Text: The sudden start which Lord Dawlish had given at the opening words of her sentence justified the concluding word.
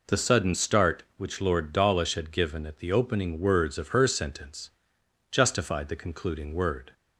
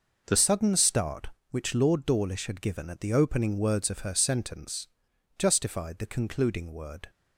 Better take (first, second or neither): first